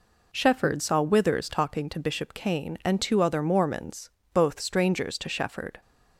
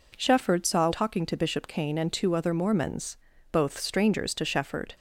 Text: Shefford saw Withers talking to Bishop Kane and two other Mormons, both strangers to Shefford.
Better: first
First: none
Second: skips "Withers"; at 0.9 s

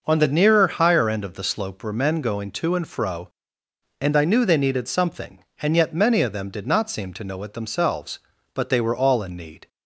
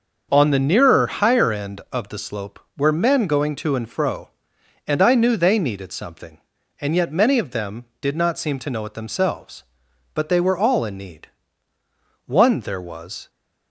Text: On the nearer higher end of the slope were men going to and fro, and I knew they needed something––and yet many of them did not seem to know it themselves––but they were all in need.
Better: first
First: none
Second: starts louder than the rest; until 1.3 s; 6.5 dB // goes on to say "One there was"; noticeable; from 12.2 s on; 1.0 s long

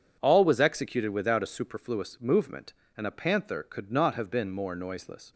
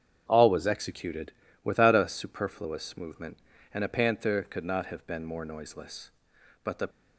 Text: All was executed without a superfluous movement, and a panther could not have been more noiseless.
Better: first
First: none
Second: starts louder than the rest; strong; until 1.2 s; 7.5 dB // pauses between "executed" and "without"; slight; at 1.3 s; 0.32 s long // goes on to say "But the"; slight; from 6.6 s on; 0.24 s long

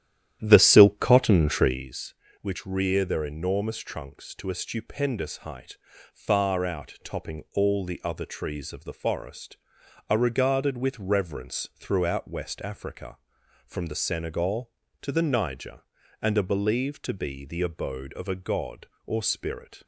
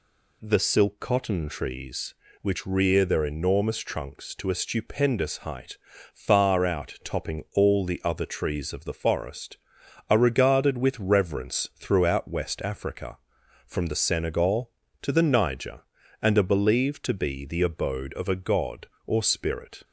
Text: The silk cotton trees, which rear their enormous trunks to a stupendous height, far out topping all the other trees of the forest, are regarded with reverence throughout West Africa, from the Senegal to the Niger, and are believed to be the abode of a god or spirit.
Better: second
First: starts louder than the rest; strong; until 1.9 s; 11.5 dB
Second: none

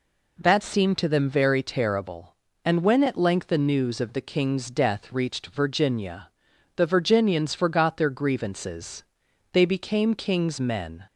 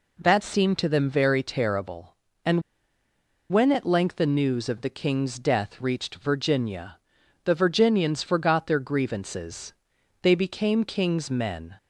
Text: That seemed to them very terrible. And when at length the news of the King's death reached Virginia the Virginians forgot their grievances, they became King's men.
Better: first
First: pauses between "Virginia" and "the"; noticeable; at 6.2 s; 0.46 s long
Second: pauses between "And" and "when"; noticeable; at 2.6 s; 0.90 s long // pauses between "Virginia" and "the"; noticeable; at 6.9 s; 0.46 s long

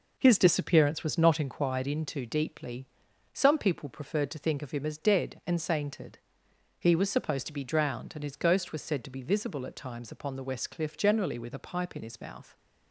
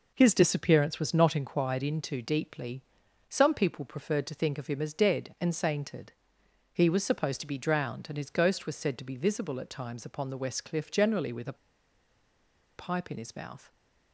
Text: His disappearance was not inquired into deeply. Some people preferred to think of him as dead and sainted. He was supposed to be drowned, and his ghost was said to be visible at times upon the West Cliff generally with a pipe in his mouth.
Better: first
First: none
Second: pauses between "a" and "pipe"; at 11.5 s; 1.2 s long

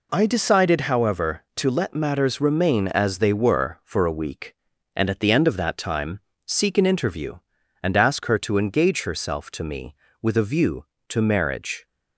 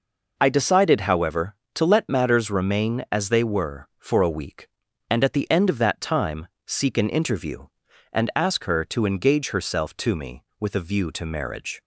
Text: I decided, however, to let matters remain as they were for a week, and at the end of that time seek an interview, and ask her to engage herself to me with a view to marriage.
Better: neither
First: pauses between "time" and "seek"; slight; at 6.1 s; 0.28 s long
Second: pauses between "time" and "seek"; slight; at 6.4 s; 0.20 s long

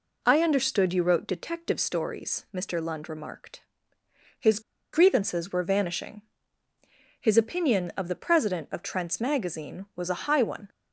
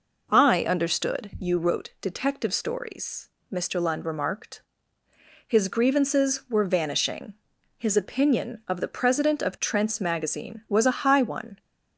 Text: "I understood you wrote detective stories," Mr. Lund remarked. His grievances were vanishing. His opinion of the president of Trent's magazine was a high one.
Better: second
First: pauses between "His" and "grievances"; slight; at 4.6 s; 0.32 s long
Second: none

